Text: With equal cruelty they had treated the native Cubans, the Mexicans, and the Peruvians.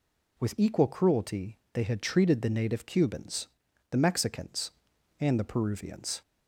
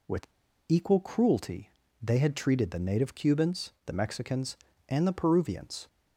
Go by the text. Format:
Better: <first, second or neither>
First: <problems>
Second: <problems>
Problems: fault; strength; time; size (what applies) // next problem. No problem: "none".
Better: first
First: pauses between "cruelty" and "they"; slight; at 1.5 s; 0.16 s long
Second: pauses between "With" and "equal"; at 0.2 s; 0.42 s long // pauses between "cruelty" and "they"; slight; at 1.7 s; 0.30 s long